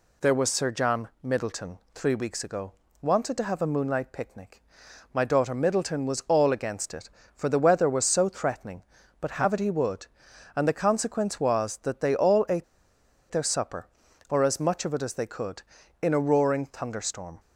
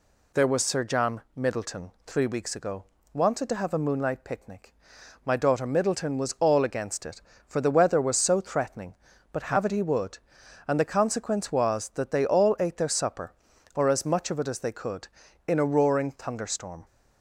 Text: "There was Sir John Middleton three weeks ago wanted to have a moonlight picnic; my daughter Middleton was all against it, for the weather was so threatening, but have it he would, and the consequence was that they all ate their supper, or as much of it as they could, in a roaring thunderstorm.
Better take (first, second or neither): second